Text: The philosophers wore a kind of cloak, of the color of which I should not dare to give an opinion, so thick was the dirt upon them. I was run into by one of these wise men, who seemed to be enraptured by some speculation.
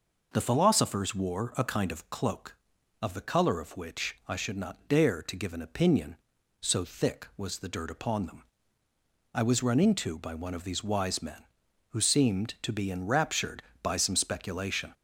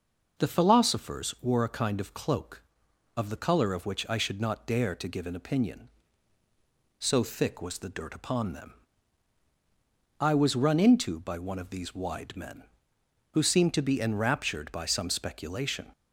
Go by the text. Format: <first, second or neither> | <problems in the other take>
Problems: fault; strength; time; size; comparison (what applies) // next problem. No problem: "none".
first | says "wide" for "wise"; at 11.9 s